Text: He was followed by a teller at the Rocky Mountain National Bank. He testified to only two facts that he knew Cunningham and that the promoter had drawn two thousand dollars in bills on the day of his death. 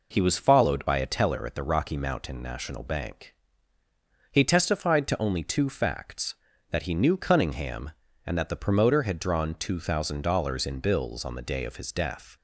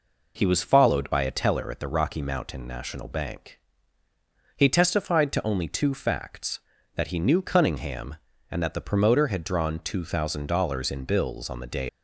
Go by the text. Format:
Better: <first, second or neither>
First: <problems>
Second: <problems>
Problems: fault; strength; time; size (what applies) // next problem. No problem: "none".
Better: first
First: none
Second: stops before "of his death"; at 11.8 s